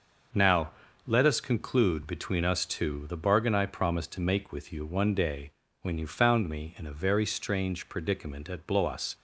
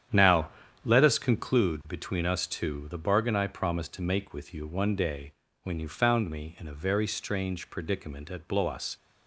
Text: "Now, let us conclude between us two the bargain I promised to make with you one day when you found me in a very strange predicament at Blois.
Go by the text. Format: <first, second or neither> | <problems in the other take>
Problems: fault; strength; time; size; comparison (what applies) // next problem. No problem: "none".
first | starts louder than the rest; strong; until 1.6 s; 9.5 dB // pauses between "day" and "when"; slight; at 5.3 s; 0.28 s long; slight in the first